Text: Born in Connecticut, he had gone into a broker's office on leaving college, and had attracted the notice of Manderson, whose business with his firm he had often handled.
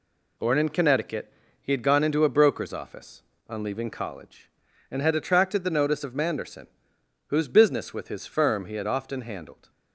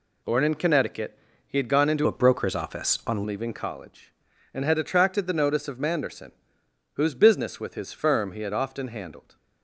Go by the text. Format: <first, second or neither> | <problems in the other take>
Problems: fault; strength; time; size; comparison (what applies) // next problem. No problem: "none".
first | changes voice from "a" to "on"; from 2.0 to 3.2 s; 1.2 s long